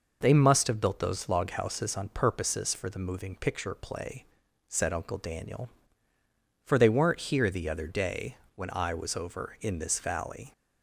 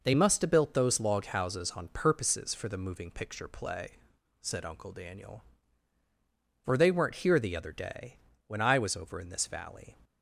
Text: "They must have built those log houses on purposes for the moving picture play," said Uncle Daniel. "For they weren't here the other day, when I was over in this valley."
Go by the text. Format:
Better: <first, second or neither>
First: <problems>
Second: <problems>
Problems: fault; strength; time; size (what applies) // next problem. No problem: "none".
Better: neither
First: none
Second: none